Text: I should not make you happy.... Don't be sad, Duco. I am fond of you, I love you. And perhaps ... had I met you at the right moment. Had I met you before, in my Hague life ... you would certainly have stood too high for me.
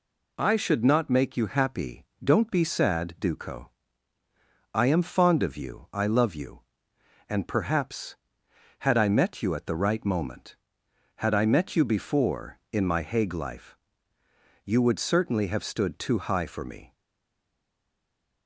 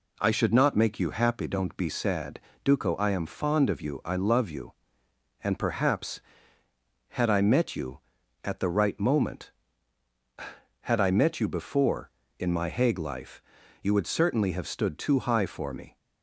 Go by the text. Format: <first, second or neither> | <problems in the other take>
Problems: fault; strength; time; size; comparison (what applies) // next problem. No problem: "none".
second | stays silent after the last word; noticeable; from 16.9 s on; 1.5 s long